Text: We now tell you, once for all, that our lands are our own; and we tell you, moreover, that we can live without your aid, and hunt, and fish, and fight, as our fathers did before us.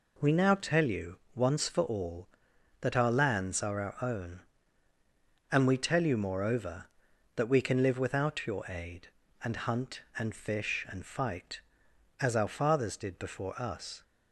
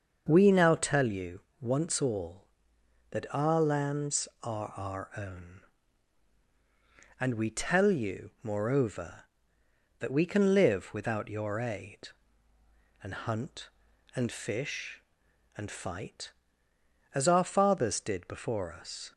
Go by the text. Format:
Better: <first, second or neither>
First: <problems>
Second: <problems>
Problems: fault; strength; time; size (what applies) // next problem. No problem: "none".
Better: first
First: none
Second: starts louder than the rest; until 1.2 s; 6.5 dB // skips "for"; at 2.0 s